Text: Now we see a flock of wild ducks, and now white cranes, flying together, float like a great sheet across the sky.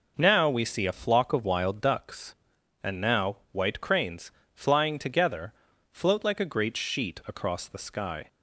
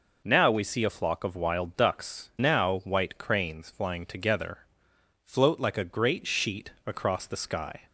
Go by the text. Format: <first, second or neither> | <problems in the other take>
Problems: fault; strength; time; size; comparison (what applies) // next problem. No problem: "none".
first | skips "and"; at 2.3 s // pauses between "sheet" and "across"; slight; at 6.7 s; 0.16 s long